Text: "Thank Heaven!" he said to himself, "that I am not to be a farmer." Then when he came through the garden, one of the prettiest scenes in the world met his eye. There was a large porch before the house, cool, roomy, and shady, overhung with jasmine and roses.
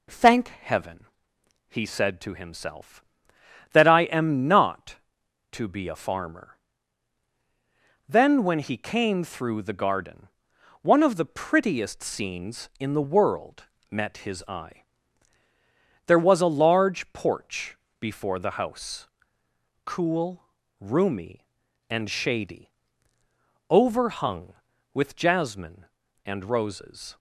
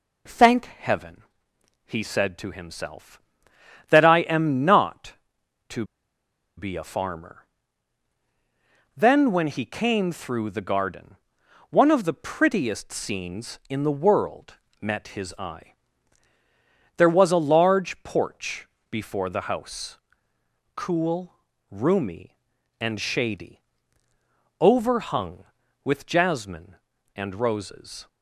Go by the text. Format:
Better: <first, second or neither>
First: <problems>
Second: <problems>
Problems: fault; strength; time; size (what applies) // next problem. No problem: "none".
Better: first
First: pauses between "world" and "met"; slight; at 13.6 s; 0.24 s long // pauses between "porch" and "before"; slight; at 17.7 s; 0.22 s long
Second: pauses between "to" and "be"; noticeable; at 5.8 s; 0.72 s long // pauses between "world" and "met"; slight; at 14.5 s; 0.24 s long // pauses between "porch" and "before"; slight; at 18.6 s; 0.22 s long